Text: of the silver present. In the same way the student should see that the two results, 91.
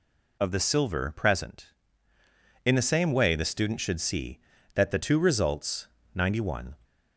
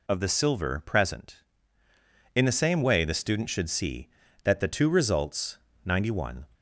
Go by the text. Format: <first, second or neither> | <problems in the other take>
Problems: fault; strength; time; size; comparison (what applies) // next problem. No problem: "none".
neither | none